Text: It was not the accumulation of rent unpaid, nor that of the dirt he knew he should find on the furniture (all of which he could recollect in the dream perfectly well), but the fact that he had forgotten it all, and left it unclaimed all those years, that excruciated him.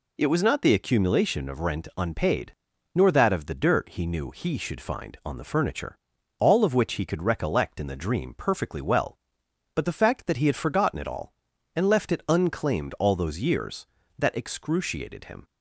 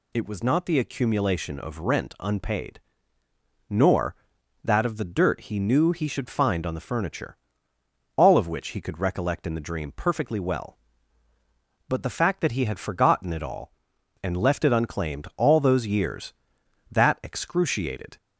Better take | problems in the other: first | stops before "him"; at 18.1 s

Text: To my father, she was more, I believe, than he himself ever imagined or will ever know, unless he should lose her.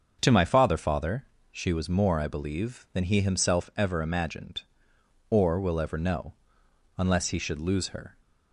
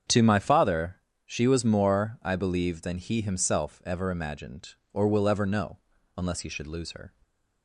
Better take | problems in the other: second | starts louder than the rest; until 1.2 s; 6.5 dB; strong in the second // says "father" twice; at 0.7 s

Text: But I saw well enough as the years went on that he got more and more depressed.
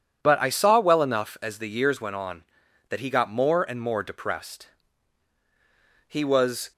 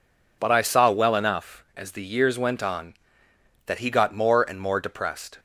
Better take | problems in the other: second | goes on to say "He was"; noticeable; from 6.0 s on; 0.64 s long

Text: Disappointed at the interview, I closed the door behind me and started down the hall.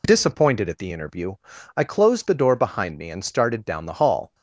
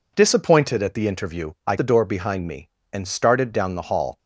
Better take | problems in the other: first | skips "closed"; at 1.7 s

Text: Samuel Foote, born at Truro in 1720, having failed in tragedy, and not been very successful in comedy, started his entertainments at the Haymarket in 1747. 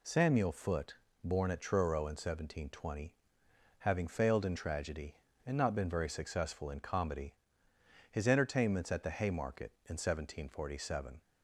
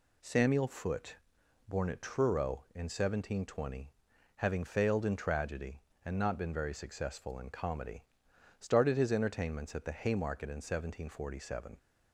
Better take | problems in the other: second | skips "started"; at 7.7 s

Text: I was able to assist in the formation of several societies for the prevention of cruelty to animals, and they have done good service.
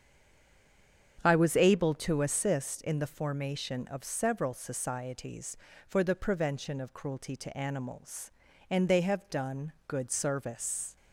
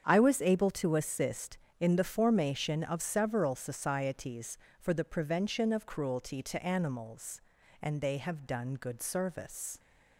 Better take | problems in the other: second | stays silent before the first word; until 1.1 s; 1.1 s long // starts louder than the rest; strong; until 2.2 s; 8 dB; strong in the second

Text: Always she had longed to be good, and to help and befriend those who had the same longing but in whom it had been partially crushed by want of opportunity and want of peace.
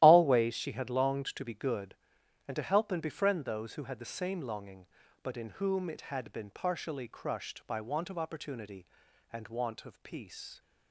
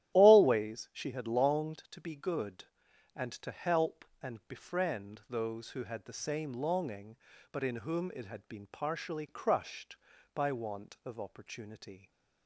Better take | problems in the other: first | starts louder than the rest; strong; until 1.1 s; 12.5 dB; strong in the first // stops before "and want of peace"; at 12.1 s

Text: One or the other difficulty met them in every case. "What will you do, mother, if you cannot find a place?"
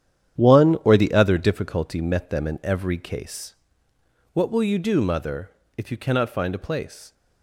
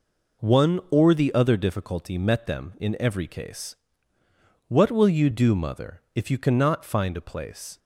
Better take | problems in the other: second | gets quieter; strong; throughout; 10.5 dB

